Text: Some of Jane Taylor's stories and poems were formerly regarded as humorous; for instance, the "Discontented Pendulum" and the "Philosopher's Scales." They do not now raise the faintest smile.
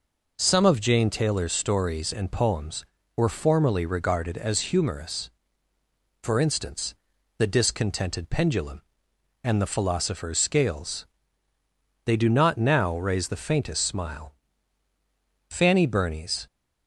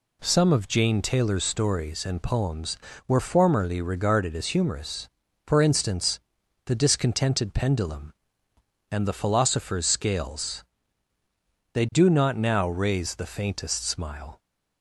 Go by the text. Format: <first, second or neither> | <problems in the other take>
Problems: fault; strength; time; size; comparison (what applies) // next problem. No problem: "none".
second | goes on to say "Fanny Burney's"; noticeable; from 15.5 s on; 0.96 s long